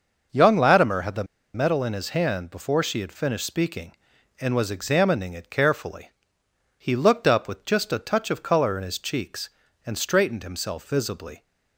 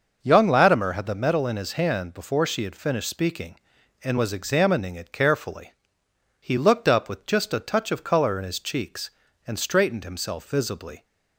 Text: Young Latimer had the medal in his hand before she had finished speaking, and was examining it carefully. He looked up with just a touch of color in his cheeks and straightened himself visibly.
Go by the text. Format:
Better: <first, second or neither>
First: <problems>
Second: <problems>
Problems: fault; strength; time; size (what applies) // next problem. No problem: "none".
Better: second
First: pauses between "the" and "medal"; slight; at 1.2 s; 0.30 s long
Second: none